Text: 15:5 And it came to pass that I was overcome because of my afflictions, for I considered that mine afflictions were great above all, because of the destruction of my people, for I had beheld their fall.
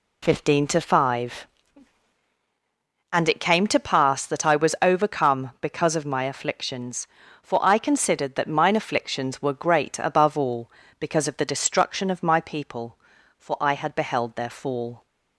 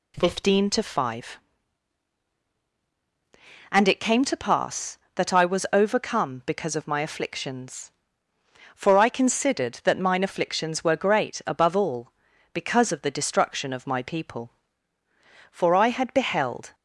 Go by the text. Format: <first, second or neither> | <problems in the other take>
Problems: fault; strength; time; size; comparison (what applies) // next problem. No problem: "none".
first | stops before "their fall"; at 16.7 s